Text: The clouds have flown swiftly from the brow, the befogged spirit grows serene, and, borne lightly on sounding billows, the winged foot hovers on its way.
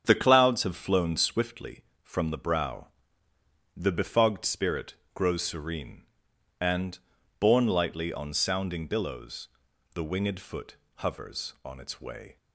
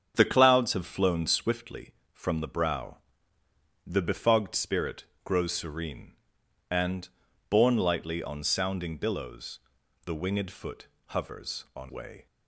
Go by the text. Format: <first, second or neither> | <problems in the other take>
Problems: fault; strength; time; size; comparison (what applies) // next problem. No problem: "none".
first | starts louder than the rest; strong; until 1.1 s; 7.5 dB; strong in the first // pauses between "spirit" and "grows"; slight; at 5.0 s; 0.22 s long; slight in the first // pauses between "foot" and "hovers"; slight; at 10.8 s; 0.22 s long; slight in the first // skips "its"; at 11.9 s